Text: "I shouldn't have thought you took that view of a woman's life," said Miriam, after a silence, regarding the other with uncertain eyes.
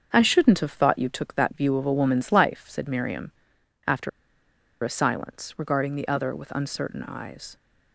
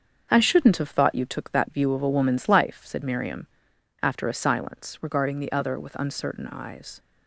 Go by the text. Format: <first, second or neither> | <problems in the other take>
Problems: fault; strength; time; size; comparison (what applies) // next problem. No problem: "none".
second | starts louder than the rest; strong; until 1.1 s; 7 dB; also in the second // pauses between "after" and "a"; noticeable; at 4.0 s; 0.72 s long